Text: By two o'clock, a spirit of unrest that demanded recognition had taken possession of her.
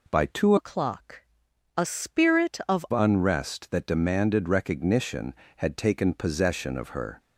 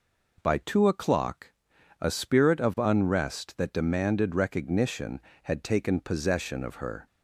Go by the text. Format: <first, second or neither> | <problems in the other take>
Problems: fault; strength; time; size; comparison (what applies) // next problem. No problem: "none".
second | changes voice from "o'clock" to "of"; from 0.5 to 2.8 s; 2.3 s long